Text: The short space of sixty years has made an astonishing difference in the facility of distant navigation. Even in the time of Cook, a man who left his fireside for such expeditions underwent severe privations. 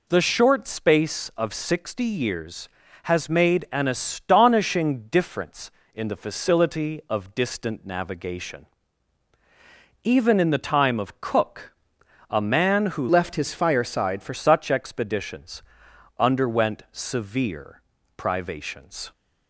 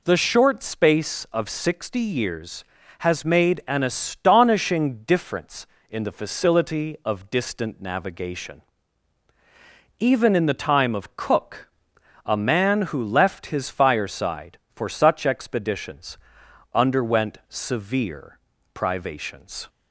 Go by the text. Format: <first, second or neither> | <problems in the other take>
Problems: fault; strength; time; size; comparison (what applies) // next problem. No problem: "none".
second | changes voice from "left" to "for"; from 13.0 to 14.3 s; 1.3 s long // pauses between "expeditions" and "underwent"; noticeable; at 15.6 s; 0.58 s long; noticeable in the second // pauses between "severe" and "privations"; slight; at 17.8 s; 0.36 s long; slight in the second